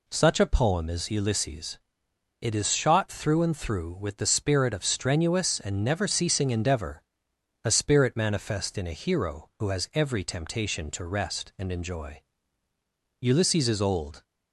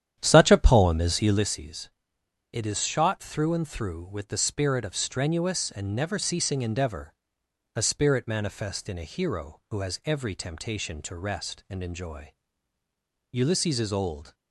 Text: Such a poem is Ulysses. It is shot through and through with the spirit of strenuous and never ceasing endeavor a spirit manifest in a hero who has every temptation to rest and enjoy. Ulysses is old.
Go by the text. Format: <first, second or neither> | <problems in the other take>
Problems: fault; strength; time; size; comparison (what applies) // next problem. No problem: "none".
first | starts louder than the rest; strong; until 1.5 s; 10 dB // pauses between "endeavor" and "a"; noticeable; at 7.1 s; 0.62 s long; noticeable in the first